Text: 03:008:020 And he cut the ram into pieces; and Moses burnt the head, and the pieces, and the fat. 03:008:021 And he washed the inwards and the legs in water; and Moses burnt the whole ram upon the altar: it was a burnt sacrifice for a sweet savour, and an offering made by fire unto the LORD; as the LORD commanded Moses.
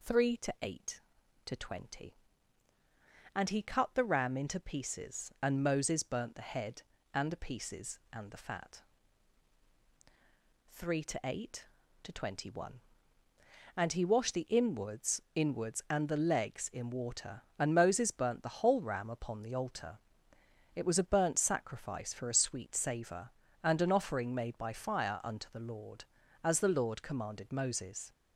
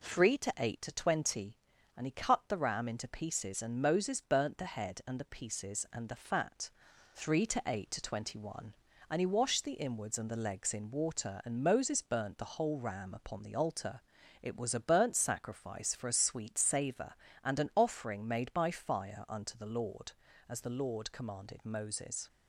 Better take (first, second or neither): second